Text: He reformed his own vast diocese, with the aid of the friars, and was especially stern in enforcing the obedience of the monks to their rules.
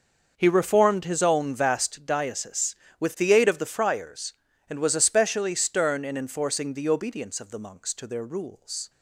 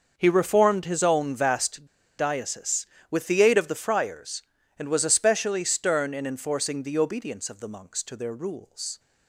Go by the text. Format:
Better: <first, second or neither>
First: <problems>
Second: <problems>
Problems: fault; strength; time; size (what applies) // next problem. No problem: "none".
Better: first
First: starts louder than the rest; noticeable; until 1.3 s; 6 dB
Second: starts louder than the rest; noticeable; until 1.1 s; 6 dB // pauses between "vast" and "diocese"; slight; at 1.8 s; 0.33 s long